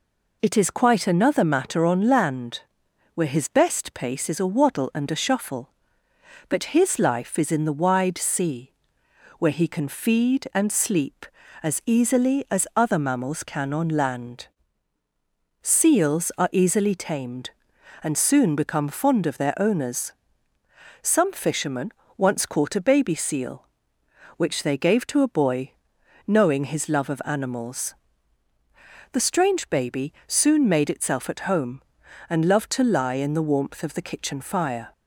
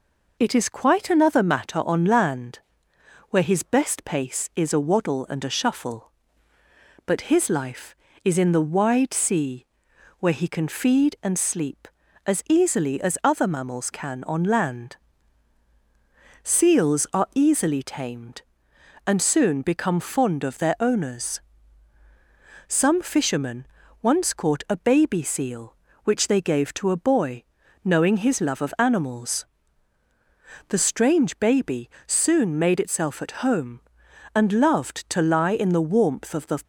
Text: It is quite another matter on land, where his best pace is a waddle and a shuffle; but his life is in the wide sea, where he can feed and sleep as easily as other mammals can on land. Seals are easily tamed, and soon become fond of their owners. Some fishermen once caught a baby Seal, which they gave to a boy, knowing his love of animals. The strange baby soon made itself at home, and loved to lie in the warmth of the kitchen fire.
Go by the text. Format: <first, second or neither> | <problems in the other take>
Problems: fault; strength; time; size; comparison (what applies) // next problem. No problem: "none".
first | pauses between "fishermen" and "once"; slight; at 23.6 s; 0.34 s long; slight in the first // pauses between "baby" and "soon"; slight; at 31.8 s; 0.16 s long // stops before "kitchen fire"; at 36.6 s